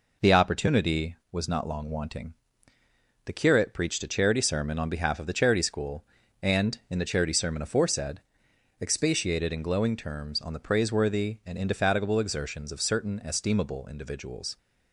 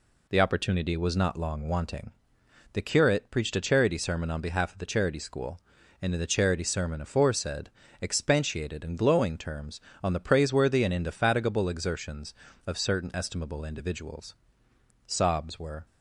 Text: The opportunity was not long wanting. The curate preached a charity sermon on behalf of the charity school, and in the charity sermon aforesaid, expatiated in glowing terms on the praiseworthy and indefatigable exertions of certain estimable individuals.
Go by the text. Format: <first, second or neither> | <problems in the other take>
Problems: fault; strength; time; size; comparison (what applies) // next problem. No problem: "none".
first | goes on to say "Sobs were"; noticeable; from 15.0 s on; 0.78 s long